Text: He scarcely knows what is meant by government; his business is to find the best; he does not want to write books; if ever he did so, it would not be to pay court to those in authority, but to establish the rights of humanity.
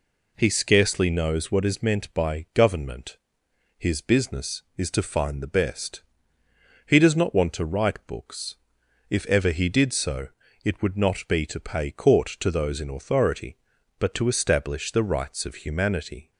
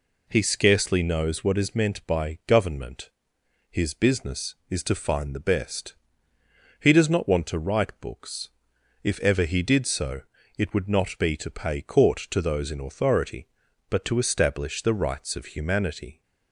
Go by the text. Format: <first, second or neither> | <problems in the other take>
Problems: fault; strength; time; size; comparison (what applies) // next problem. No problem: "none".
neither | none